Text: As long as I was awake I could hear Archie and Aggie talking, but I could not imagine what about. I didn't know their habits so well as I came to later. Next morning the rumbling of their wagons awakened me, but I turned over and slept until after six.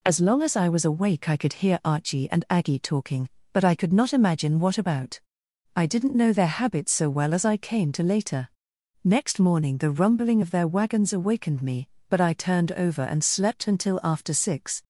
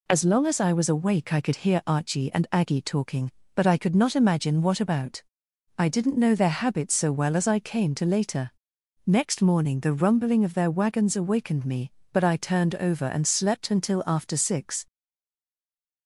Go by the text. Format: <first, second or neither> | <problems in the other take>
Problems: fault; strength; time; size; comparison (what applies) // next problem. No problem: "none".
first | stays silent after the last word; noticeable; from 14.8 s on; 1.2 s long